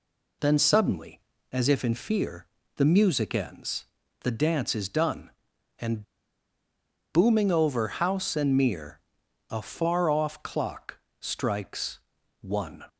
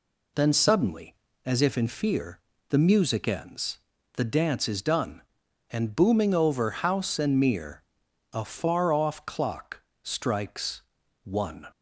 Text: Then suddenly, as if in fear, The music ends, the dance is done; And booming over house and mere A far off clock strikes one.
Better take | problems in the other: second | pauses between "And" and "booming"; at 6.0 s; 1.1 s long // pauses between "mere" and "A"; noticeable; at 8.9 s; 0.50 s long; noticeable in the second // pauses between "clock" and "strikes"; slight; at 10.9 s; 0.22 s long; slight in the second // pauses between "strikes" and "one"; at 11.9 s; 0.42 s long; also in the second

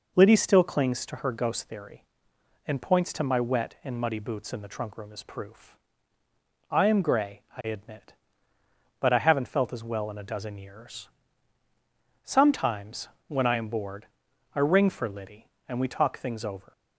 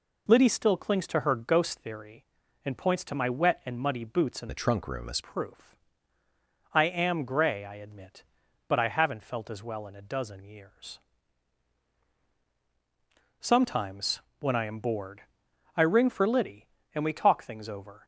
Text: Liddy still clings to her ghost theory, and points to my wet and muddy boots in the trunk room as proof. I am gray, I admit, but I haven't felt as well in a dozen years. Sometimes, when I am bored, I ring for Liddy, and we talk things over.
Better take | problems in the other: first | changes voice from "the" to "as"; from 4.4 to 5.1 s; 0.7 s long

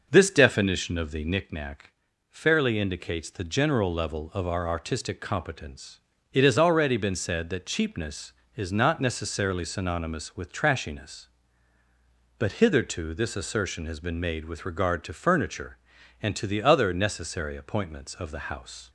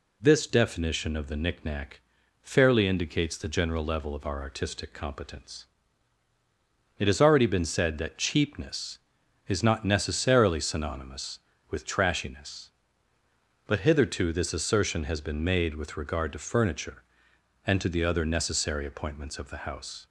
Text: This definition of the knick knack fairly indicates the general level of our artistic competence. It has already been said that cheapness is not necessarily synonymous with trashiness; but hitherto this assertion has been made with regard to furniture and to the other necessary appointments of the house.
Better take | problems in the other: second | starts louder than the rest; noticeable; until 1.4 s; 6 dB // pauses between "knack" and "fairly"; at 1.9 s; 0.38 s long; also in the second

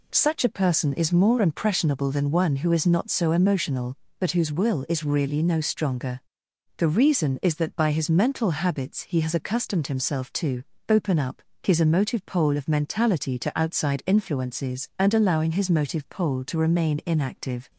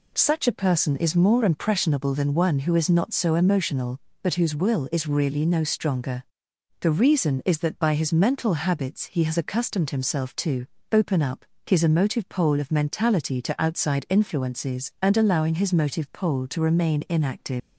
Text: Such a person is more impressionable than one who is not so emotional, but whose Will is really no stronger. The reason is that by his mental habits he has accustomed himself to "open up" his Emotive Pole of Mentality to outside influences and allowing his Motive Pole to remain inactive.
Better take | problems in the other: first | pauses between "to" and "open"; slight; at 10.6 s; 0.24 s long; slight in the first // pauses between "up" and "his"; slight; at 11.4 s; 0.20 s long; slight in the first // leaves "inactive" unfinished; at 17.6 s; 130 ms

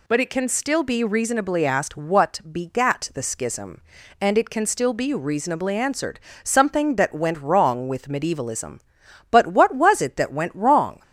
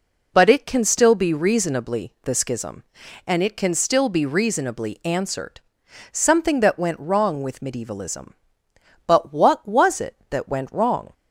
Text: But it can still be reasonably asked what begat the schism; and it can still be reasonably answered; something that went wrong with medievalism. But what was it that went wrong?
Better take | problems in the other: first | skips "asked what begat"; at 2.1 s

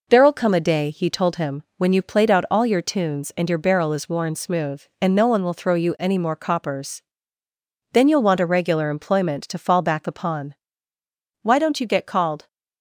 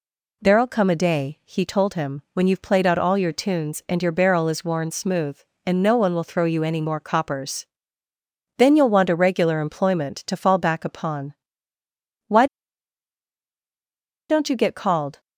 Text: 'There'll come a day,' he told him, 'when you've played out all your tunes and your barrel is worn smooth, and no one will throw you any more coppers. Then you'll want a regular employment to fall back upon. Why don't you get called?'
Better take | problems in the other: first | pauses between "Why" and "don't"; strong; at 12.4 s; 1.8 s long

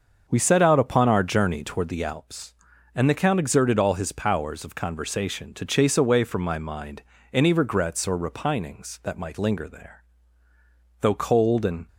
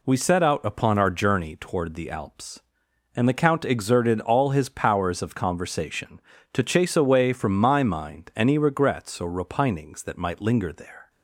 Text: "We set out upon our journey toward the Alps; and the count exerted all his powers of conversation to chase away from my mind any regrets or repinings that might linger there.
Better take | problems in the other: second | starts louder than the rest; until 1.2 s; 6.5 dB // pauses between "mind" and "any"; slight; at 7.0 s; 0.30 s long // goes on to say "Though cold and"; noticeable; from 10.9 s on; 0.88 s long

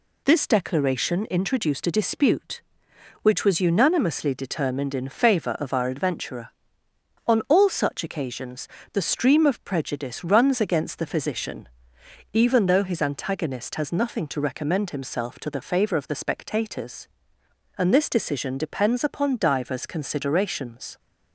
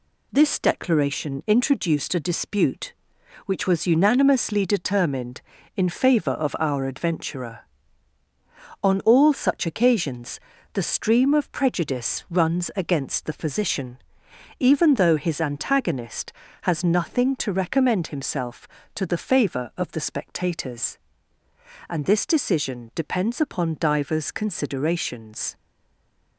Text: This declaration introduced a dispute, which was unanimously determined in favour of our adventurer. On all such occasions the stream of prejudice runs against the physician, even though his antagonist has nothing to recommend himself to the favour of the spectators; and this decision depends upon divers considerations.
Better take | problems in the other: first | pauses between "occasions" and "the"; slight; at 10.3 s; 0.36 s long; slight in the first // stays silent after the last word; slight; from 25.5 s on; 0.8 s long

